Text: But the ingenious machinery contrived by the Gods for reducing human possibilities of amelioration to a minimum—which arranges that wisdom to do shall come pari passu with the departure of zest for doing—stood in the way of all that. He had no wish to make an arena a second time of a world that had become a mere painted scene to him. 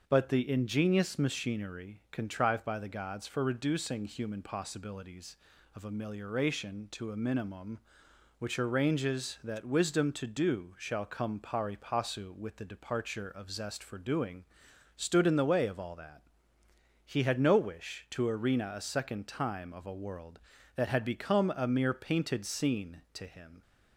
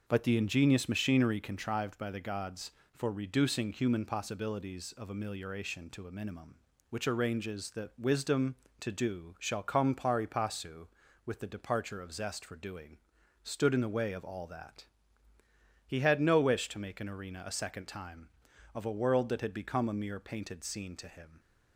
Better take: second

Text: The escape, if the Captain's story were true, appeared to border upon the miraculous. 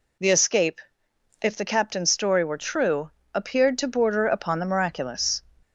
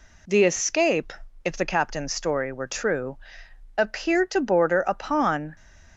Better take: first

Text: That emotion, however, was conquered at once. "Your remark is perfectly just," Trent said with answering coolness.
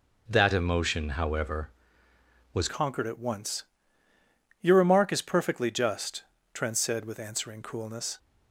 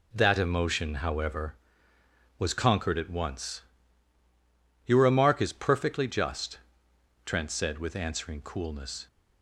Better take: second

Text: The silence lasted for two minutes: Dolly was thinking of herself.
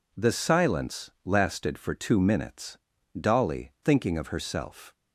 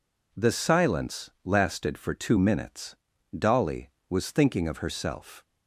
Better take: second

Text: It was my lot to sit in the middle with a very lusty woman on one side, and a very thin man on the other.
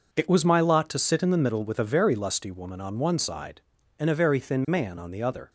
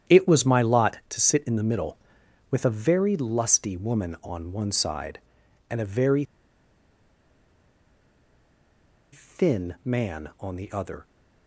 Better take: first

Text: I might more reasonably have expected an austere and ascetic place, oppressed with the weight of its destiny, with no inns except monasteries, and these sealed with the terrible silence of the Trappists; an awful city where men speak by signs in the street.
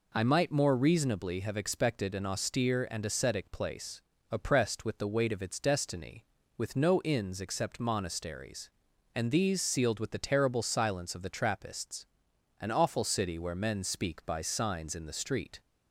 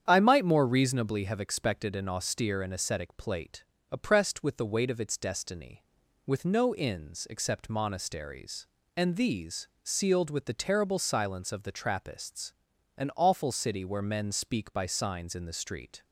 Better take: first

